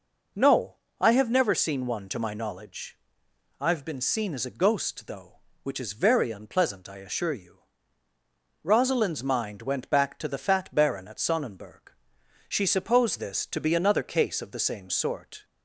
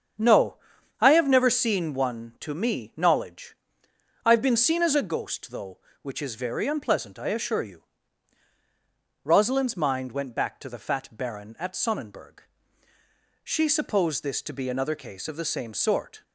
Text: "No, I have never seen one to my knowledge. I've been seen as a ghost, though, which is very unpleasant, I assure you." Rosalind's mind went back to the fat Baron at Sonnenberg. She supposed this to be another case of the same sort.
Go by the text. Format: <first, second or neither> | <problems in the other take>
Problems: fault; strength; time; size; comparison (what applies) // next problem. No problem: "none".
first | starts louder than the rest; strong; until 1.6 s; 7.5 dB // says "me" for "my"; at 2.5 s